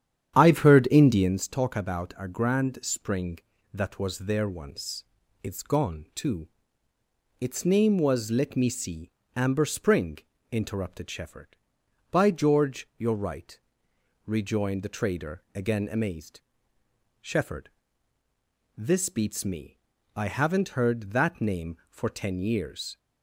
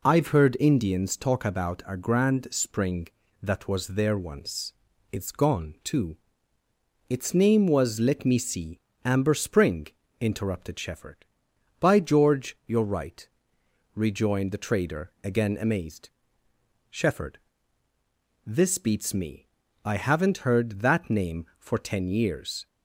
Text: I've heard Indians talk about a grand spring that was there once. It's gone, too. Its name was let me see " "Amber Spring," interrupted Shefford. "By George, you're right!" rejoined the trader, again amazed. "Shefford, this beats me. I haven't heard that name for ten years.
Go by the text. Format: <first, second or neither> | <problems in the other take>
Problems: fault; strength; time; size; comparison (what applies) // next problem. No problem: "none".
second | starts louder than the rest; strong; until 1.4 s; 9.5 dB